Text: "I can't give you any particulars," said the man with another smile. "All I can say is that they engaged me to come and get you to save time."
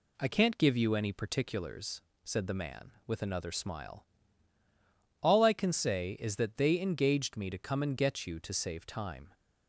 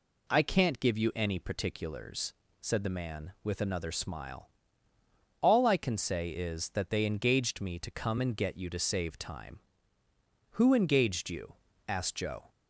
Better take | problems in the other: first | goes on to say "Who engaged you asked Joe"; strong; from 10.5 s on; 1.9 s long

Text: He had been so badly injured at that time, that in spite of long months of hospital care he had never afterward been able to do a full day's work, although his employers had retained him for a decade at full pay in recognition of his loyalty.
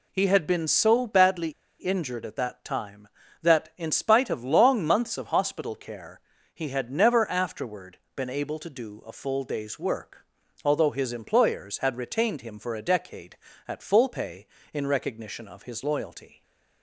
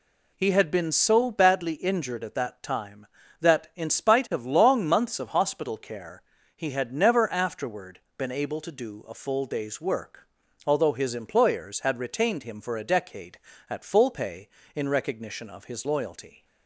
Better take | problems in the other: second | pauses between "badly" and "injured"; slight; at 1.5 s; 0.28 s long // pauses between "care" and "he"; slight; at 6.2 s; 0.32 s long; slight in the second // pauses between "afterward" and "been"; slight; at 7.9 s; 0.18 s long; slight in the second

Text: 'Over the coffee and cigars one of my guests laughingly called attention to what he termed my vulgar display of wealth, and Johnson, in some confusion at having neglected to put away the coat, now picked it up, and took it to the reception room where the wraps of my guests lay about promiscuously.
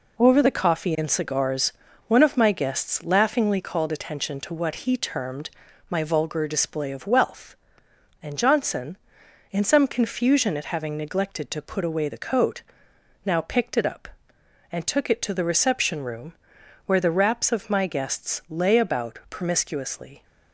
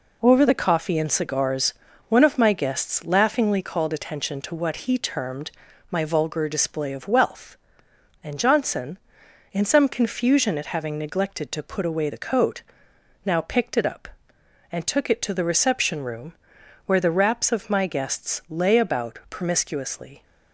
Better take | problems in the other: neither | pauses between "cigars" and "one"; slight; the same in both // pauses between "termed" and "my"; the same in both // pauses between "room" and "where"; noticeable; the same in both

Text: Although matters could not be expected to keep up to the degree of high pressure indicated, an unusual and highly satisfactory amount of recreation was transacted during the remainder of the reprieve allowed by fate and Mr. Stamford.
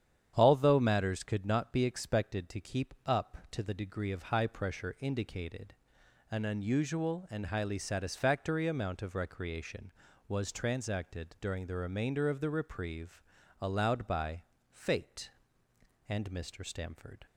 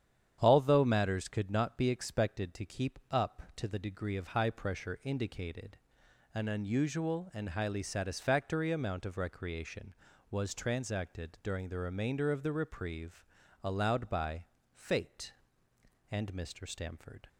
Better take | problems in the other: neither | starts louder than the rest; strong; the same in both // pauses between "reprieve" and "allowed"; the same in both // pauses between "by" and "fate"; slight; the same in both

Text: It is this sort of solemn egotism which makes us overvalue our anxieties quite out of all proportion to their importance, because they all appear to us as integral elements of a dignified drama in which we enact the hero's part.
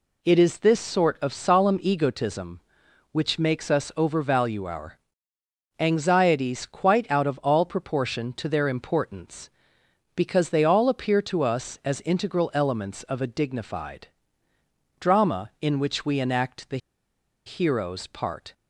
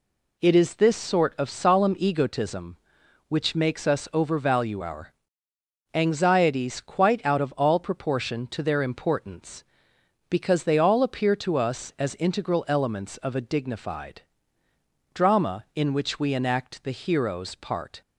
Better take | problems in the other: second | pauses between "our" and "anxieties"; noticeable; at 4.9 s; 0.80 s long; noticeable in the second // pauses between "dignified" and "drama"; noticeable; at 14.0 s; 0.90 s long; noticeable in the second // pauses between "the" and "hero's"; noticeable; at 16.7 s; 0.69 s long

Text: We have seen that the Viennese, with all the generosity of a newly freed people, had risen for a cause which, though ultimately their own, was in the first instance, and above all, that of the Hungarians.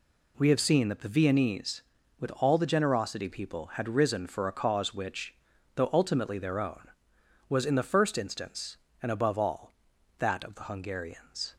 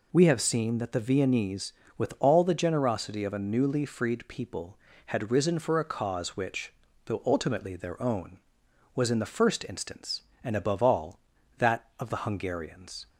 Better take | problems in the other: second | skips "of a newly freed"; at 3.2 s

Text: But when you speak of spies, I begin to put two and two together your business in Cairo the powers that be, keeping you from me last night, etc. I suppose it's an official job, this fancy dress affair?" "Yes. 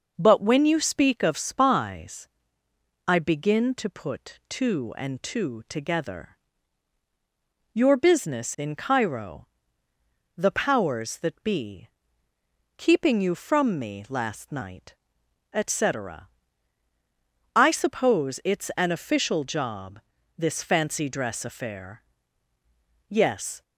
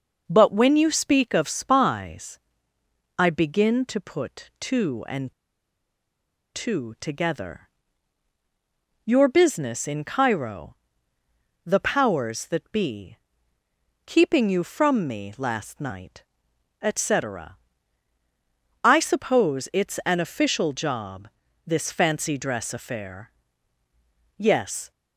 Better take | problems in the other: first | pauses between "and" and "two"; at 5.3 s; 1.2 s long // pauses between "together" and "your"; strong; at 7.6 s; 1.4 s long; strong in the first // pauses between "Cairo" and "the"; noticeable; at 10.7 s; 0.90 s long; noticeable in the first

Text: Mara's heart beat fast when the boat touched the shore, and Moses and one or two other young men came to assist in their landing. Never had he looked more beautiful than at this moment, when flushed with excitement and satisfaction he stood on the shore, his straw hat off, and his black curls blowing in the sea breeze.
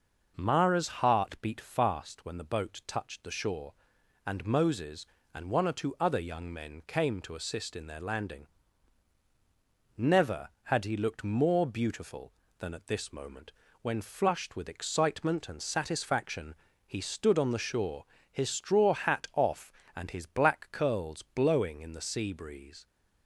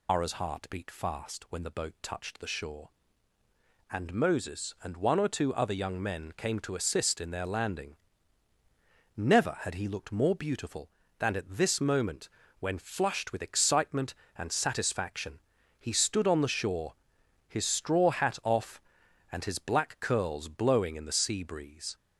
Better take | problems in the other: first | loses the start of "Mara's"; at 0.0 s; 145 ms // pauses between "satisfaction" and "he"; at 15.3 s; 0.40 s long; slight in the first

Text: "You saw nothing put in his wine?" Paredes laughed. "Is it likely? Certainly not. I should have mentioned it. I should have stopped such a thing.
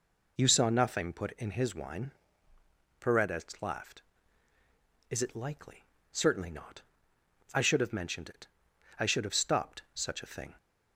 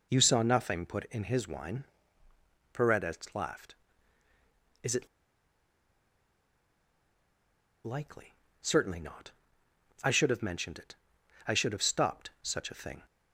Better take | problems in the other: first | pauses between "it" and "likely"; strong; at 5.0 s; 2.7 s long

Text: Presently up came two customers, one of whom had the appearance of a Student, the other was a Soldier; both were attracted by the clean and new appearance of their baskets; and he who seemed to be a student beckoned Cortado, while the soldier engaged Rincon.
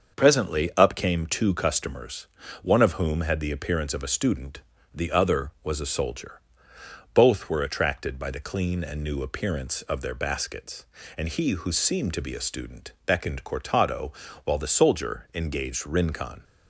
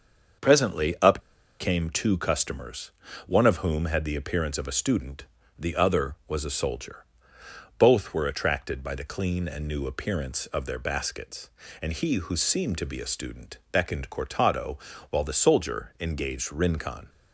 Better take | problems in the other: first | starts louder than the rest; until 1.9 s; 6.5 dB; also in the first // pauses between "up" and "came"; at 1.1 s; 0.41 s long

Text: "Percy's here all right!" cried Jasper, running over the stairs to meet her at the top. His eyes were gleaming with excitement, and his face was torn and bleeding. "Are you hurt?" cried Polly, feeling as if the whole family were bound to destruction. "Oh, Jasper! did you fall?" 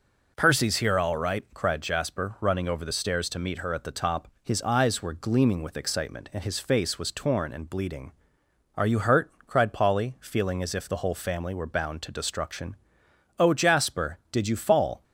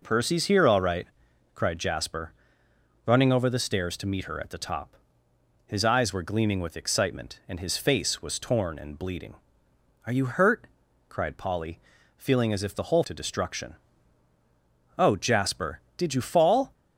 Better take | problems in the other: first | skips "family were bound"; at 13.0 s

